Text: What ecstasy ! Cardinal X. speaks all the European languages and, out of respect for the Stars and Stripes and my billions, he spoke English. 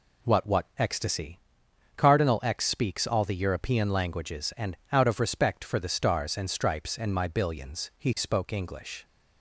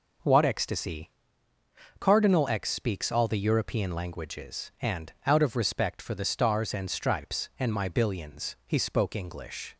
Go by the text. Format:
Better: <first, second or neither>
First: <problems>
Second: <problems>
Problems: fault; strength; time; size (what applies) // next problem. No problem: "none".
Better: second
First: says "What" twice; at 0.4 s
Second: none